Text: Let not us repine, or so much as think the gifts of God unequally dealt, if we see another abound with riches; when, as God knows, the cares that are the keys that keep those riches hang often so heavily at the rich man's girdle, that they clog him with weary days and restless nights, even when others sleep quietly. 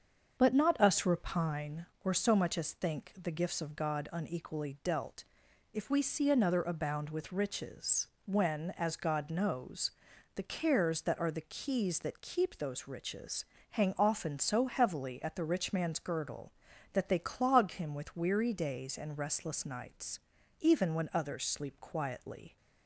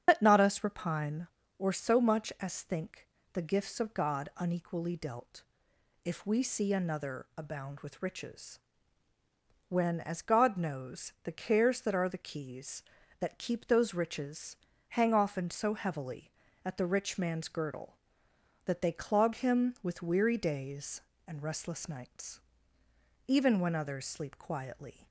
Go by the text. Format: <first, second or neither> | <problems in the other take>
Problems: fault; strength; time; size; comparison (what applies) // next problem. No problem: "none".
first | loses the start of "Let"; at 0.0 s; 100 ms // starts louder than the rest; strong; until 1.0 s; 8 dB; also in the first // pauses between "think" and "the"; slight; at 3.0 s; 0.26 s long // pauses between "riches" and "hang"; slight; at 14.5 s; 0.32 s long; slight in the first